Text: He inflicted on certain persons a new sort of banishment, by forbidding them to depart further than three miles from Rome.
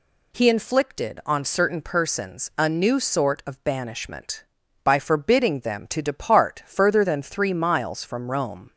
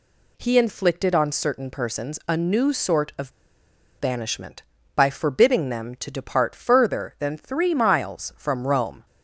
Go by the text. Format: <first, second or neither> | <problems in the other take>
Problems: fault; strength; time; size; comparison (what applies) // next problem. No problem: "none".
first | pauses between "of" and "banishment"; noticeable; at 3.3 s; 0.69 s long